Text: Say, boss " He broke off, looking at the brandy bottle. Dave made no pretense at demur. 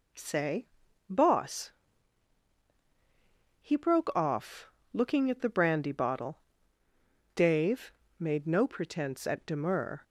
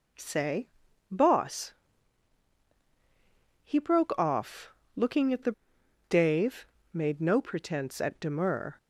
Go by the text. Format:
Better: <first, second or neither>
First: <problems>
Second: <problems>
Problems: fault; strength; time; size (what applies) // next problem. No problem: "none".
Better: first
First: pauses between "Dave" and "made"; slight; at 7.9 s; 0.26 s long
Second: skips "brandy bottle"; at 5.8 s // pauses between "Dave" and "made"; slight; at 6.6 s; 0.26 s long